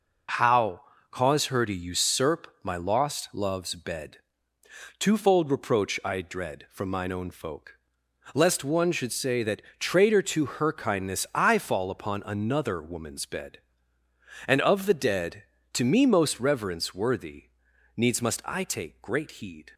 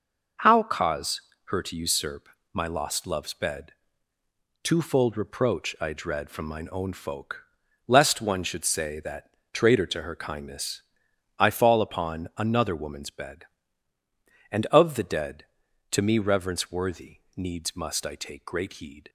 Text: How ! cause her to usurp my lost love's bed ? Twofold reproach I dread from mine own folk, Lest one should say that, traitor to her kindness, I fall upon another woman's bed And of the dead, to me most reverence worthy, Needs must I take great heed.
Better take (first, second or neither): first